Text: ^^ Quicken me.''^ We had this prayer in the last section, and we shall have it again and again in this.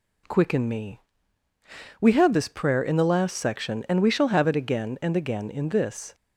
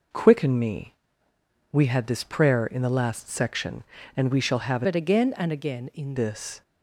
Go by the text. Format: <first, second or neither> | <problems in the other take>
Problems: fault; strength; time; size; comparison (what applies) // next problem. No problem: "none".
first | changes voice from "it" to "in"; from 4.8 to 6.1 s; 1.3 s long